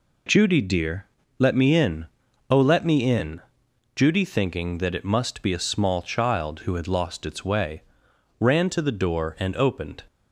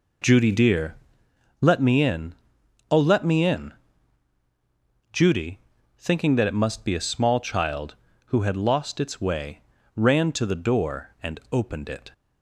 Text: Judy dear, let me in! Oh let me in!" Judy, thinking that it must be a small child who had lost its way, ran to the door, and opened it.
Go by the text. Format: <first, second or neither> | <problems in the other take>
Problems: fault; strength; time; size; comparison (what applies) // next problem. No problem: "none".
second | stops before "it"; at 10.0 s